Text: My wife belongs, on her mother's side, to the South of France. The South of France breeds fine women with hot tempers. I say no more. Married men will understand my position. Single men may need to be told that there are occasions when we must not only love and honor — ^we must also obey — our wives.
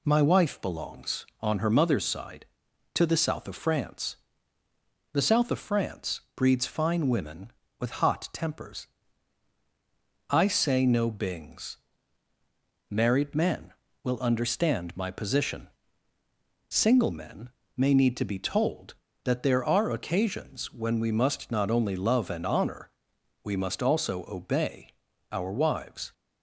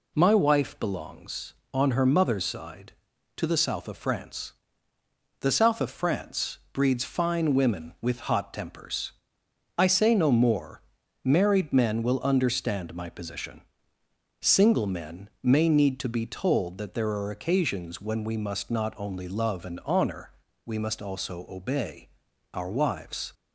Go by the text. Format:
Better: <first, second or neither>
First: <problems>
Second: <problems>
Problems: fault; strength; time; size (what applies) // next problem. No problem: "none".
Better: second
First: pauses between "France" and "breeds"; slight; at 6.1 s; 0.16 s long // says "bings" for "more"; at 11.0 s // pauses between "men" and "may"; slight; at 17.5 s; 0.26 s long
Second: pauses between "France" and "breeds"; slight; at 6.5 s; 0.16 s long